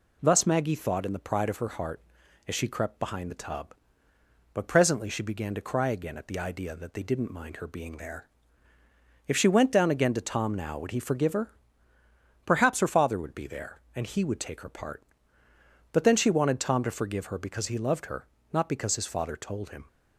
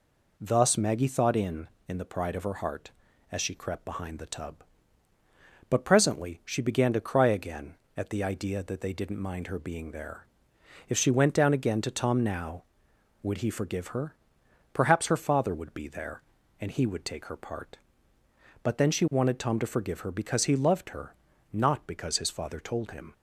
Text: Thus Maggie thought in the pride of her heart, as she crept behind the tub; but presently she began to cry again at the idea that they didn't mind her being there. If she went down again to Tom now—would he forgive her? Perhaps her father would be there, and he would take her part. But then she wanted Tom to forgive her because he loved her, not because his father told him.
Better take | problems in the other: first | says "in" twice; at 1.8 s

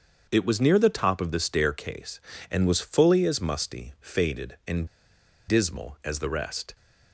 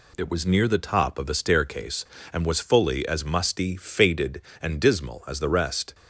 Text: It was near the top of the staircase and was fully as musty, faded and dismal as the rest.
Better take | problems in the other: second | starts louder than the rest; until 1.3 s; 6.5 dB // pauses between "and" and "dismal"; noticeable; at 4.8 s; 0.62 s long

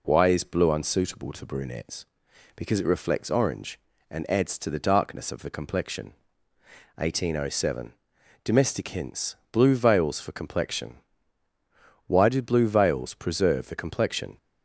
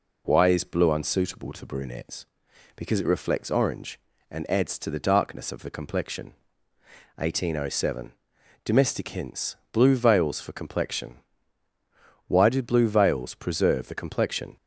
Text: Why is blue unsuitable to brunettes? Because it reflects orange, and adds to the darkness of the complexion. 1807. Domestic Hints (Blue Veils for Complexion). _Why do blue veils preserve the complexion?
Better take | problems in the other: neither | none

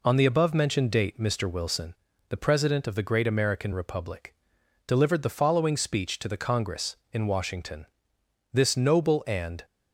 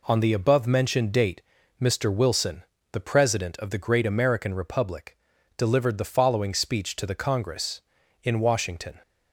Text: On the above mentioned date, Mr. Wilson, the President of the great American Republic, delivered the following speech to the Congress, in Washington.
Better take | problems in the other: second | goes on to say "This noble and"; noticeable; from 8.5 s on; 1.1 s long

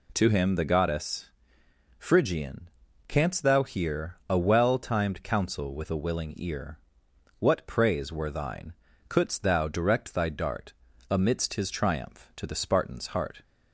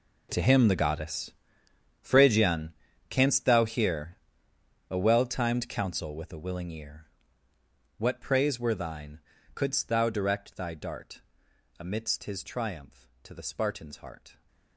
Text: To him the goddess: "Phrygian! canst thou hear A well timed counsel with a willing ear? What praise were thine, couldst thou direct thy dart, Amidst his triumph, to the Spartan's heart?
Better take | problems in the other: first | gets quieter; strong; throughout; 15.5 dB // pauses between "hear" and "A"; noticeable; at 4.1 s; 0.72 s long

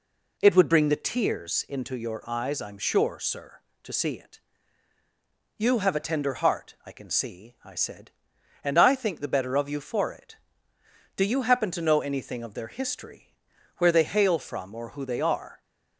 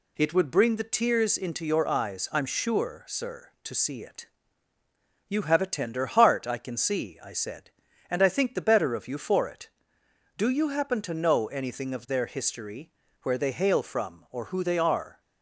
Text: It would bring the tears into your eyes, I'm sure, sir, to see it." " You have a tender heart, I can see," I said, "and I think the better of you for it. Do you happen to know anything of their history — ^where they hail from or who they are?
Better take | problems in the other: neither | none

